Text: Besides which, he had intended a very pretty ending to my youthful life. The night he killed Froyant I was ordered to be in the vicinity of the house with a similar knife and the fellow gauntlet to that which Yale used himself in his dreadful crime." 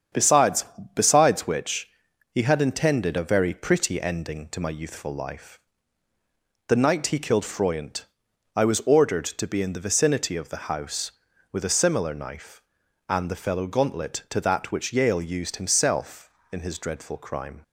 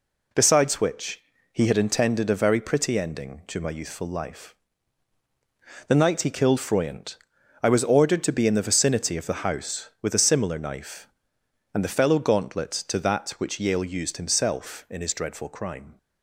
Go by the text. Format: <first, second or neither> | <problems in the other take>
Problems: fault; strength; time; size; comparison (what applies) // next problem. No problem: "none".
second | starts louder than the rest; strong; until 1.4 s; 8 dB // says "Besides" twice; at 0.9 s // pauses between "Froyant" and "I"; noticeable; at 8.0 s; 0.50 s long; also in the second